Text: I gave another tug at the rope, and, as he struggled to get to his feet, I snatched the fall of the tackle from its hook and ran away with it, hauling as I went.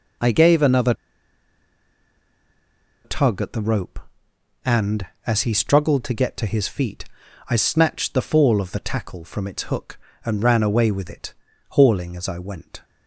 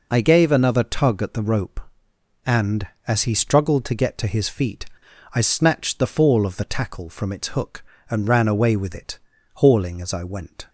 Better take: second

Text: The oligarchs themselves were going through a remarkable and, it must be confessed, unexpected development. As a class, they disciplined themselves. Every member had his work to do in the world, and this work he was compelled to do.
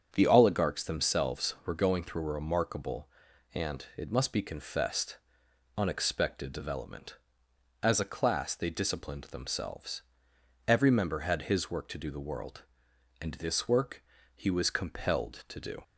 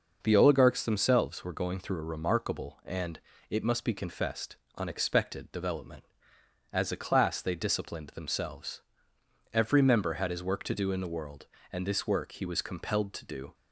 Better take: second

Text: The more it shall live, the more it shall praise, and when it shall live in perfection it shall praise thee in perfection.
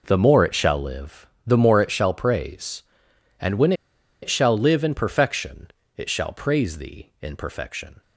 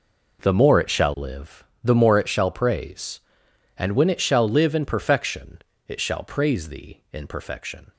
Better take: second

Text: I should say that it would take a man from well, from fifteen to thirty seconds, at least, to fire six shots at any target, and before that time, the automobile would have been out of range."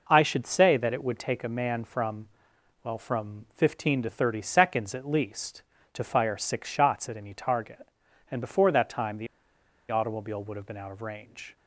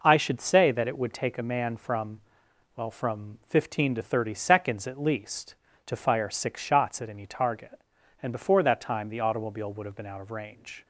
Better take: second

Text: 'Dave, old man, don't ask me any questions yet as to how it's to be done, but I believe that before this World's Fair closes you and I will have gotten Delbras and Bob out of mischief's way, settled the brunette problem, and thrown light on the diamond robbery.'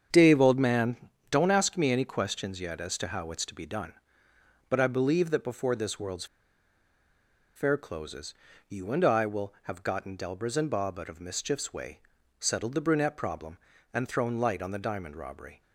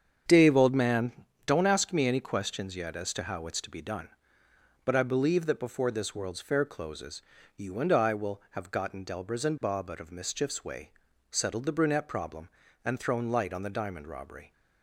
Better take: second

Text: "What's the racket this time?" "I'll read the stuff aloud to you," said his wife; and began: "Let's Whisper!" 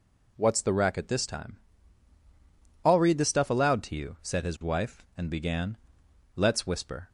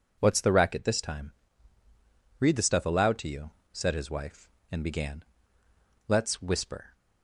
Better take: first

